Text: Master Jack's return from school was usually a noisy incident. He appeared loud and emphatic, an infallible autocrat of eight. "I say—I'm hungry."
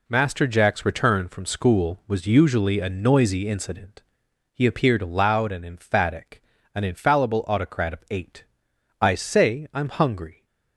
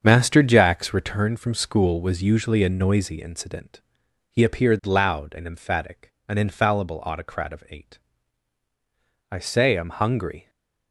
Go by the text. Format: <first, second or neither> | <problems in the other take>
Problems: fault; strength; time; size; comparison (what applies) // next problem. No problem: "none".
first | starts louder than the rest; strong; until 1.4 s; 7 dB // stays silent after the last word; slight; from 10.4 s on; 0.5 s long